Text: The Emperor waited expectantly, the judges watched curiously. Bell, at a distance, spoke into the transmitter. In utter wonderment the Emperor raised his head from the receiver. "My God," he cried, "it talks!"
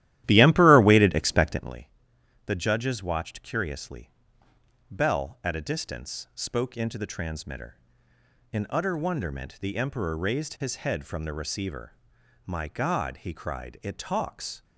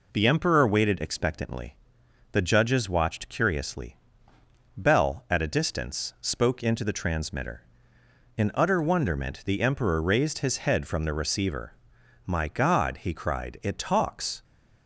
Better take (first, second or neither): second